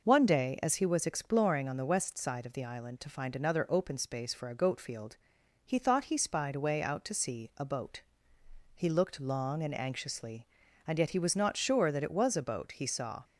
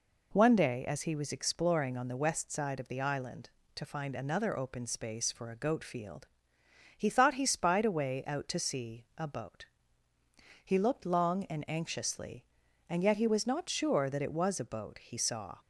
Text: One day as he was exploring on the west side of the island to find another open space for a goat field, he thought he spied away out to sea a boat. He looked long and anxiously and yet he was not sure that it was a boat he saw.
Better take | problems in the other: neither | none

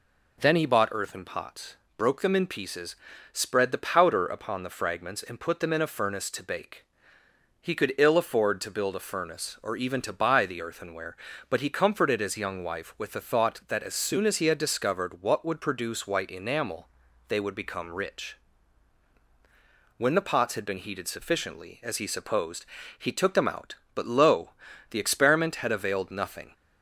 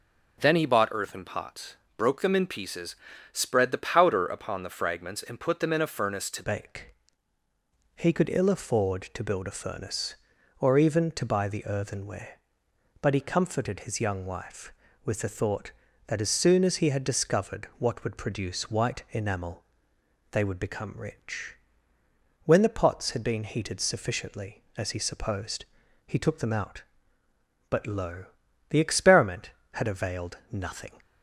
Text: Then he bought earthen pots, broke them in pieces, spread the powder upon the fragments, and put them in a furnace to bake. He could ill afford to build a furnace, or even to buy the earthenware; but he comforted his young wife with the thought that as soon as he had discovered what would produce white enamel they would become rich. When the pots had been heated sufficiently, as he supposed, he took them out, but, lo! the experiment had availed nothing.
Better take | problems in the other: first | starts louder than the rest; noticeable; until 1.4 s; 6 dB // changes voice at "bake"; from 6.4 s on; 24.5 s long // pauses between "enamel" and "they"; noticeable; at 19.6 s; 0.68 s long; also in the first

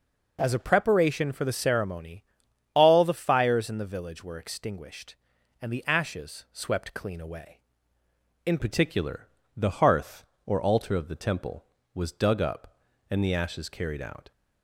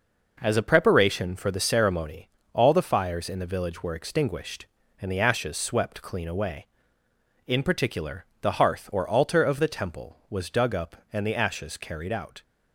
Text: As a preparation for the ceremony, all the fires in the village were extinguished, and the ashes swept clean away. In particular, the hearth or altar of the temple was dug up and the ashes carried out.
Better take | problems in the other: second | changes voice at "particular"; from 8.5 s on; 5.8 s long

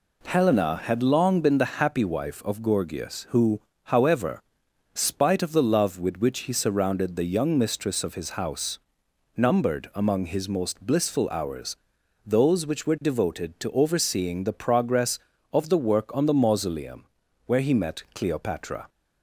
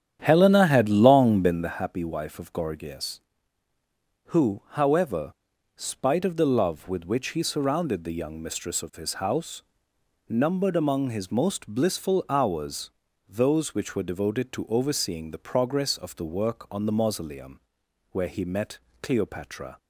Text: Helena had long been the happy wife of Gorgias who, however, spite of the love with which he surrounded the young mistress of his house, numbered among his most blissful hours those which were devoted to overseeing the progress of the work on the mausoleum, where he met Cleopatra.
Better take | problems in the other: first | starts louder than the rest; strong; until 1.8 s; 9.5 dB // pauses between "hours" and "those"; at 12.8 s; 0.40 s long; noticeable in the first // pauses between "met" and "Cleopatra"; slight; at 18.7 s; 0.24 s long

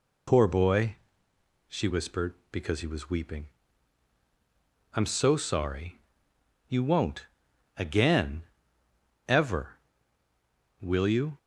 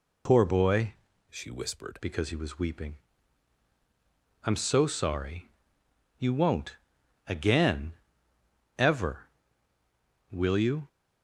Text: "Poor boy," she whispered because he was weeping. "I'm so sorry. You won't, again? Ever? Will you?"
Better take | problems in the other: first | changes voice from "she" to "whispered"; from 1.3 to 1.9 s; 0.6 s long

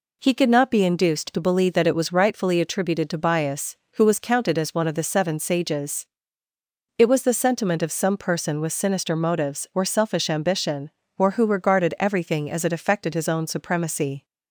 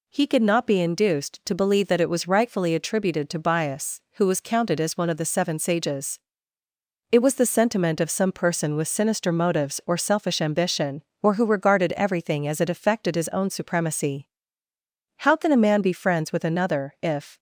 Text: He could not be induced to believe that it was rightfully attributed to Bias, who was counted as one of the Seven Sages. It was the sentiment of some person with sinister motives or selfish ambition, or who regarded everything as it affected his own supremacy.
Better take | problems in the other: first | goes on to say "How can a man be friends with another if"; strong; from 15.2 s on; 2.1 s long

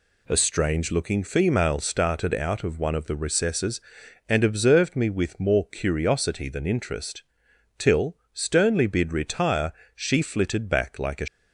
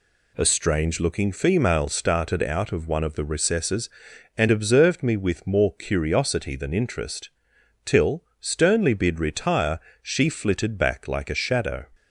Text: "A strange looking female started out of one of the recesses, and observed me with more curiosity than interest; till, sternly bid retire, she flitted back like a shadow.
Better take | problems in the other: second | stops before "shadow"; at 11.2 s

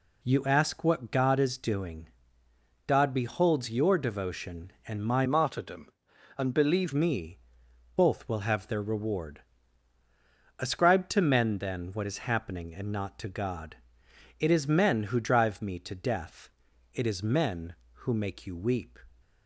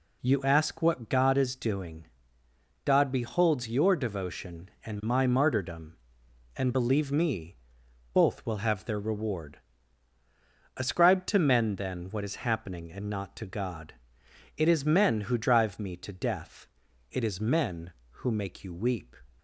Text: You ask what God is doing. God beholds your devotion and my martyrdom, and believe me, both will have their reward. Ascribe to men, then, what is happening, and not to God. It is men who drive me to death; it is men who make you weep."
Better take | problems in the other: second | changes voice from "martyrdom" to "believe"; from 5.2 to 6.9 s; 1.7 s long

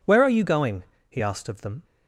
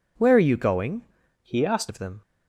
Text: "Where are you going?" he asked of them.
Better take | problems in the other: first | changes voice from "he" to "asked"; from 1.4 to 1.8 s; 0.4 s long

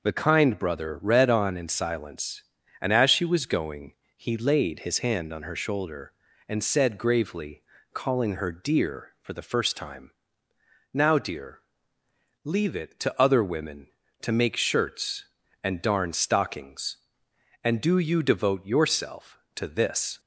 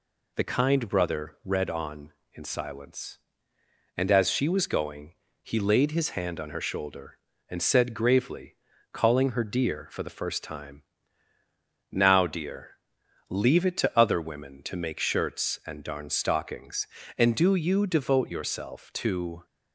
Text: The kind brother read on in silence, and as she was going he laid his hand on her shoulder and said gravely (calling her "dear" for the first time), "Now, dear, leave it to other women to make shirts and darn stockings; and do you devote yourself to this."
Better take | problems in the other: first | pauses between "going" and "he"; slight; at 5.1 s; 0.30 s long; slight in the first // stops before "this"; at 19.4 s

